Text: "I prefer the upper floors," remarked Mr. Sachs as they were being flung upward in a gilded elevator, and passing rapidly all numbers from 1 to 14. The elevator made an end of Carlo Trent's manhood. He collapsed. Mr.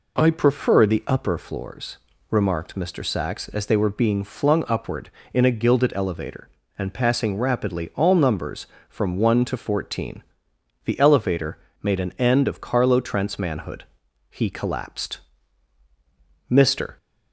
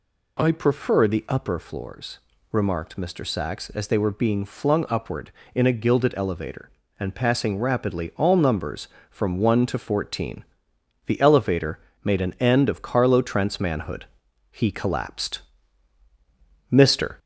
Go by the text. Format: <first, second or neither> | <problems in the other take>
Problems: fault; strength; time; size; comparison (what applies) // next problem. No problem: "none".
first | gets louder; slight; throughout; 3 dB // pauses between "elevator" and "made"; slight; at 11.8 s; 0.24 s long; slight in the first